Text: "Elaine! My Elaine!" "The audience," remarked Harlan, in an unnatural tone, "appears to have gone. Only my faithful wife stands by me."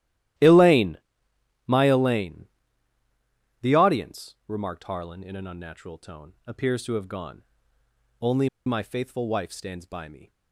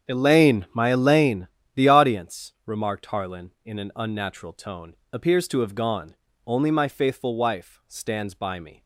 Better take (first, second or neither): second